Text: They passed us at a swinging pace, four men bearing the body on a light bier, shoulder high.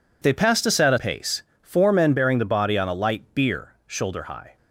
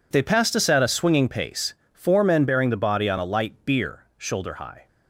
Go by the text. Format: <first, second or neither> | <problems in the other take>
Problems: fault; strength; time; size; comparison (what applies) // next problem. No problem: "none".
second | skips "swinging"; at 0.9 s